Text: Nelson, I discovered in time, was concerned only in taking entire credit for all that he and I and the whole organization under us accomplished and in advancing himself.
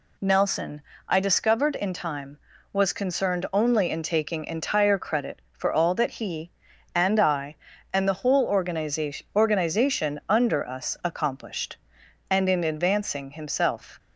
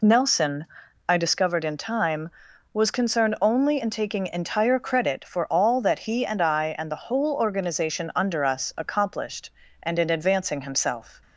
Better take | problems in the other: second | says "organization" twice; at 9.3 s

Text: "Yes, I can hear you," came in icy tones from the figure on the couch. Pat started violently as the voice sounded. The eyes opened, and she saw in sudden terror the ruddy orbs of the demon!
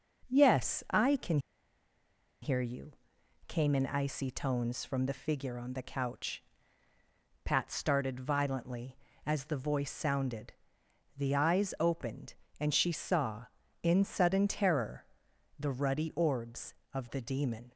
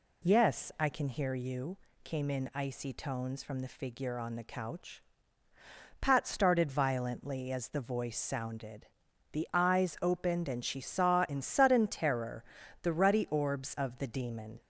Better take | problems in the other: second | pauses between "can" and "hear"; at 1.3 s; 1.0 s long // pauses between "terror" and "the"; noticeable; at 15.0 s; 0.54 s long; also in the second

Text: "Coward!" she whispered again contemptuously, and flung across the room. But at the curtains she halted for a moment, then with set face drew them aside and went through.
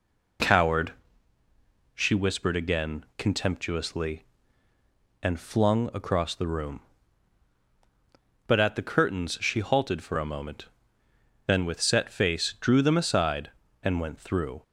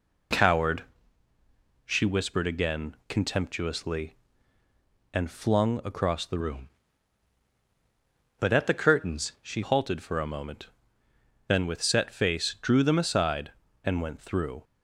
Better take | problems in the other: first | changes voice from "room" to "she"; from 6.3 to 9.6 s; 3.3 s long

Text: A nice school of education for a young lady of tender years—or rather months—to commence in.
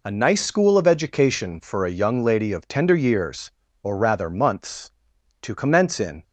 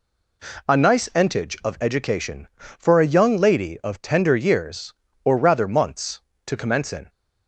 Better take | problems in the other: first | says "entage" for "school"; at 1.1 s

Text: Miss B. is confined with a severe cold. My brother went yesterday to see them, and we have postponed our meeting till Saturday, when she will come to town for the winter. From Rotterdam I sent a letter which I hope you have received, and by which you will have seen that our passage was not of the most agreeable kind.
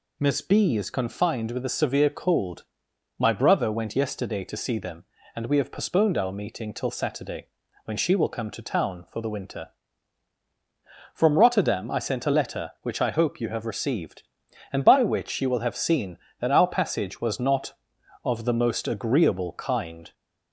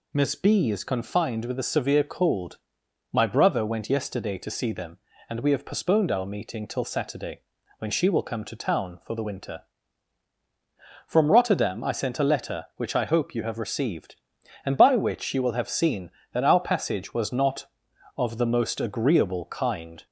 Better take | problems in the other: neither | none

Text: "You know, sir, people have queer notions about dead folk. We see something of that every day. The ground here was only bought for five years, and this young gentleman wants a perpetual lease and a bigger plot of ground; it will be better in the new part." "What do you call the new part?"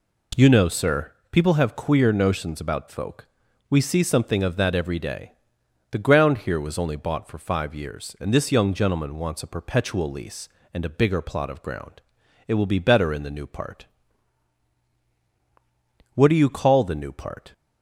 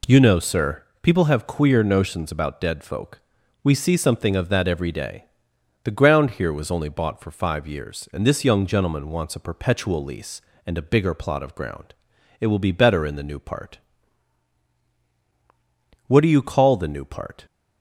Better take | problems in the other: second | skips "dead"; at 2.8 s

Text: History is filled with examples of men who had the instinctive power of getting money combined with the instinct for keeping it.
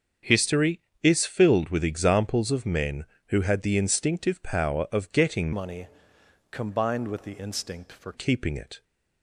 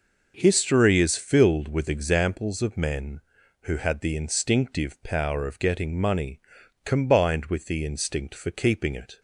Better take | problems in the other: second | starts louder than the rest; strong; until 1.4 s; 7 dB // changes voice from "money" to "for"; from 5.5 to 8.1 s; 2.6 s long // pauses between "money" and "combined"; noticeable; at 5.8 s; 0.62 s long; also in the second

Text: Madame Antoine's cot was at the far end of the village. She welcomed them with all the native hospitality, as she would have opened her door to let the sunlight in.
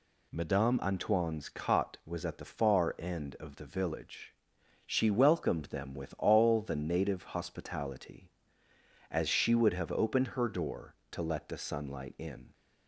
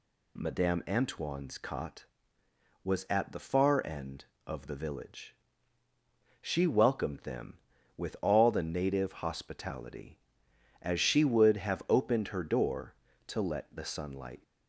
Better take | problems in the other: first | stops before "in"; at 14.4 s

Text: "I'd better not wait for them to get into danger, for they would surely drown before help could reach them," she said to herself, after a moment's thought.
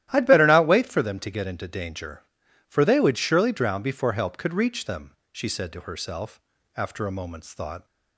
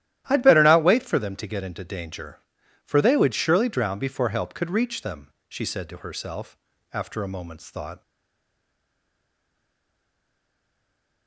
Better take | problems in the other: first | starts louder than the rest; strong; until 1.2 s; 12.5 dB; strong in the first // stays silent after the last word; strong; from 8.0 s on; 3.2 s long

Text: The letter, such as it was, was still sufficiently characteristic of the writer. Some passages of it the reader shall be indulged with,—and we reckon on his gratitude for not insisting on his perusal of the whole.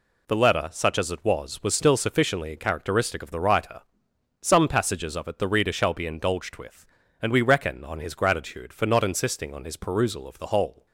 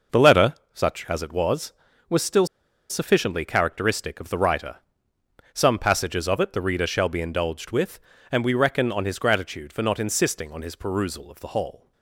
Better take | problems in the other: first | pauses between "still" and "sufficiently"; at 2.4 s; 0.44 s long

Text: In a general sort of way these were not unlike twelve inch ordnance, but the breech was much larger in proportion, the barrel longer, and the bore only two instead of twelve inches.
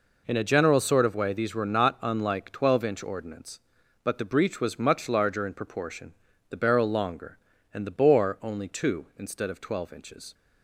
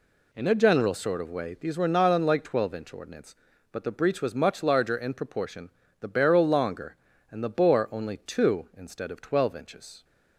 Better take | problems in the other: neither | none

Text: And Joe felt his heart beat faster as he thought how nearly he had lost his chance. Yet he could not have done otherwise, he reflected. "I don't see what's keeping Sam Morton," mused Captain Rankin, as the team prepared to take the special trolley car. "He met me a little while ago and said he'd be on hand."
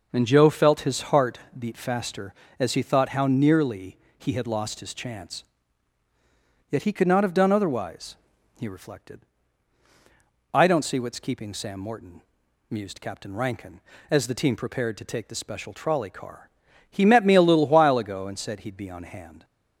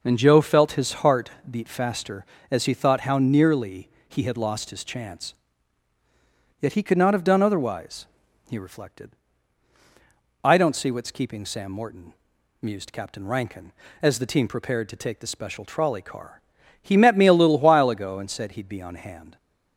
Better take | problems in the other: neither | pauses between "heart" and "beat"; slight; the same in both // pauses between "nearly" and "he"; slight; the same in both

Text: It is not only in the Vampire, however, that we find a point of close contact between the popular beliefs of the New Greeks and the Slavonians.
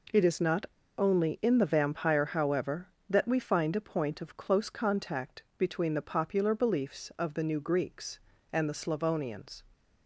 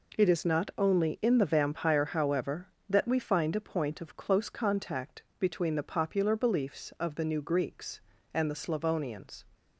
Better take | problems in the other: second | pauses between "not" and "only"; slight; at 0.6 s; 0.33 s long // pauses between "contact" and "between"; slight; at 5.4 s; 0.16 s long; slight in the second

